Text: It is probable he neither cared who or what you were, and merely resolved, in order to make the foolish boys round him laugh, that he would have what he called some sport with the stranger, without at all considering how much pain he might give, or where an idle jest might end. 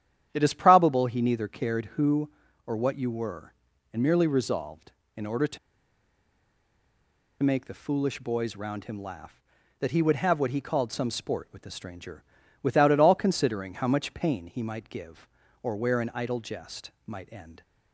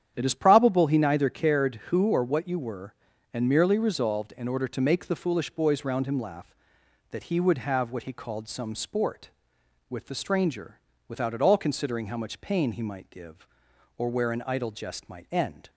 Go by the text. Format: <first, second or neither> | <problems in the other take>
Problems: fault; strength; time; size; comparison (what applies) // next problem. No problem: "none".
second | starts louder than the rest; strong; until 1.3 s; 10.5 dB; strong in the second // pauses between "to" and "make"; strong; at 5.5 s; 1.8 s long // pauses between "jest" and "might"; slight; at 16.9 s; 0.16 s long